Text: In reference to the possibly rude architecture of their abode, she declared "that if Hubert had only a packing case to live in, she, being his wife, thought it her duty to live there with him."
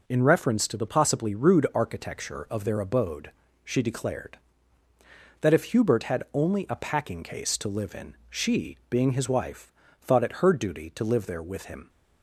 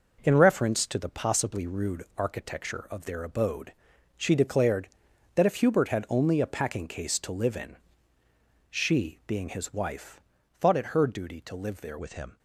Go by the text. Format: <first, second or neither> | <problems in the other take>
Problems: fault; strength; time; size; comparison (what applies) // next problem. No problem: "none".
first | changes voice at "with"; from 11.9 s on; 0.4 s long